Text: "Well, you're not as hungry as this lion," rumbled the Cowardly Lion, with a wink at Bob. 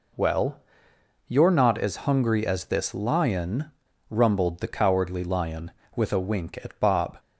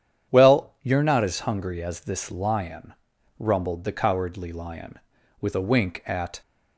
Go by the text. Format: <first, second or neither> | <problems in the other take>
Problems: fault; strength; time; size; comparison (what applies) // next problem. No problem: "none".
first | starts louder than the rest; strong; until 1.3 s; 9 dB // stops before "Bob"; at 6.4 s